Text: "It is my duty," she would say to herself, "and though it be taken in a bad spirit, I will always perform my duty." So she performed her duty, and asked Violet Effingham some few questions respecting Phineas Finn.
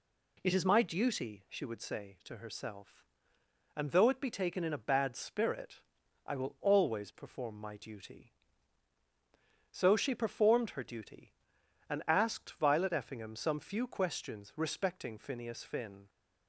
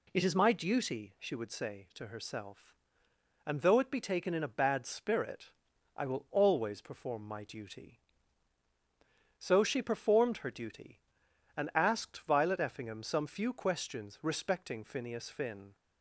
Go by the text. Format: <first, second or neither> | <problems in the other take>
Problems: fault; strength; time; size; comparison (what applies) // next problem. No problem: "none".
neither | none